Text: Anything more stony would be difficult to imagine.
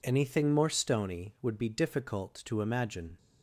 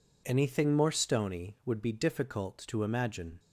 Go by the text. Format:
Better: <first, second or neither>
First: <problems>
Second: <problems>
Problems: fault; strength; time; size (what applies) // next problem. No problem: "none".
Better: neither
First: none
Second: none